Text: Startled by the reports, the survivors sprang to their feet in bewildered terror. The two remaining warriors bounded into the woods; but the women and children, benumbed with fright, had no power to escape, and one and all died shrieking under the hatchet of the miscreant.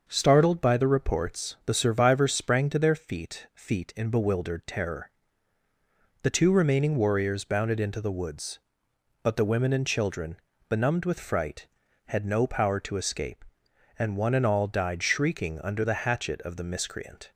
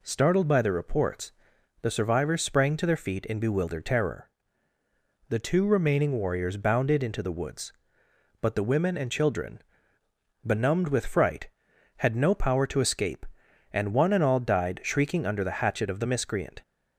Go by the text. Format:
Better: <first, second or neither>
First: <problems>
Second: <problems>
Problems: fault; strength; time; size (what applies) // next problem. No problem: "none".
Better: second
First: starts louder than the rest; until 1.0 s; 6.5 dB // says "feet" twice; at 3.5 s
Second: none